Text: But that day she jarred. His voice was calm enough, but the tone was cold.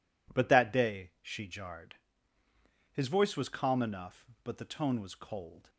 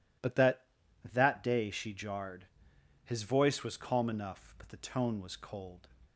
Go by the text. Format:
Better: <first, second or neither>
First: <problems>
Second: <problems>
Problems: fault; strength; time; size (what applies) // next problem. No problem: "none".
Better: first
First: none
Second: says "that" twice; at 1.1 s